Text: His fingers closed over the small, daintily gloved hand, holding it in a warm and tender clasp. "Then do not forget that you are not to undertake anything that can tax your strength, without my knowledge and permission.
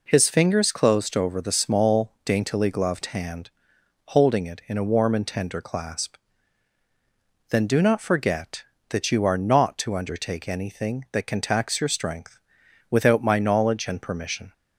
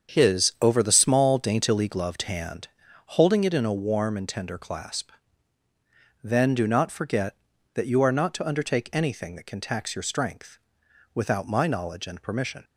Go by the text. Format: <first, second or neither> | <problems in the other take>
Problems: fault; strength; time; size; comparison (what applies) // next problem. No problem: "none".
first | starts louder than the rest; strong; until 1.1 s; 7.5 dB // skips "fingers closed"; at 0.5 s